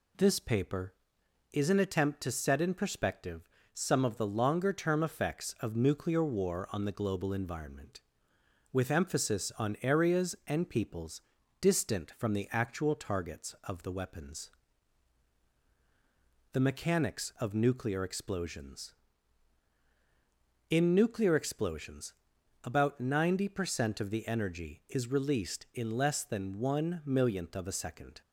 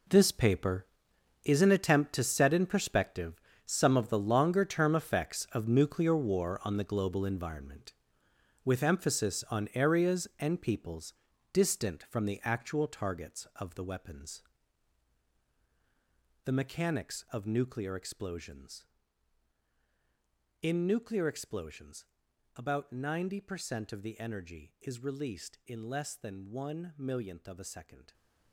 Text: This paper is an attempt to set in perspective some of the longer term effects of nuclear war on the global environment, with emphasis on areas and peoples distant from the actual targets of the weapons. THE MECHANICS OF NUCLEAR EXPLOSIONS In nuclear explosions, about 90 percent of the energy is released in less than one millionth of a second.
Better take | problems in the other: first | gets quieter; strong; throughout; 13 dB // pauses between "perspective" and "some"; slight; at 3.4 s; 0.24 s long; slight in the first // pauses between "peoples" and "distant"; at 11.1 s; 0.38 s long; also in the first

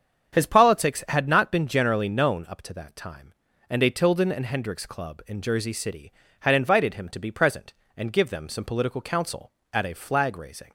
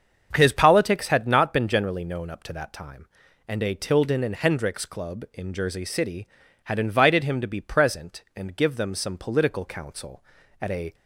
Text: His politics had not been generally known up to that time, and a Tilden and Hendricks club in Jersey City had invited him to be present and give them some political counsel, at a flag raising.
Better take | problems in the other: first | starts louder than the rest; until 1.3 s; 7 dB; strong in the first // stops before "flag raising"; at 10.9 s

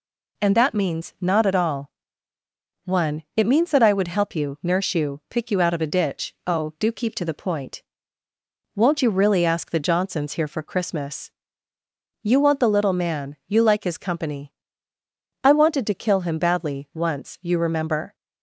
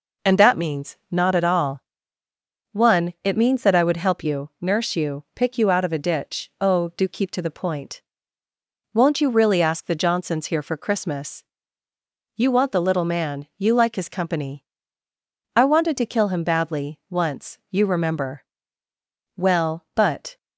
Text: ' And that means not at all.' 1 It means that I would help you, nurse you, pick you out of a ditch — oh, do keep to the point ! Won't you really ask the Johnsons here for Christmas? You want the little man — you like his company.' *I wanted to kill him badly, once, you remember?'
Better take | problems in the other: first | goes on to say "Well but"; noticeable; from 19.3 s on; 1.0 s long

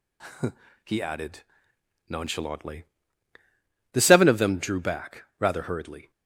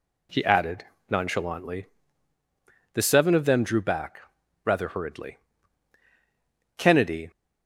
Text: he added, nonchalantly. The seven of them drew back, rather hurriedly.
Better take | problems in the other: first | goes on to say "Kennedy"; from 6.7 s on; 0.52 s long

